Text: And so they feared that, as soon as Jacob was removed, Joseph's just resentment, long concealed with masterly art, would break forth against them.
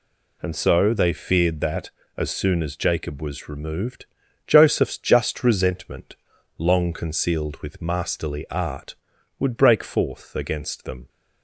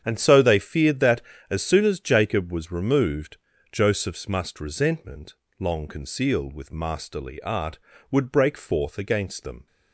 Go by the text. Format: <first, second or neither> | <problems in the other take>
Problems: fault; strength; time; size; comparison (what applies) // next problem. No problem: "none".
first | starts louder than the rest; strong; until 1.0 s; 8 dB // says "must" for "just"; at 4.2 s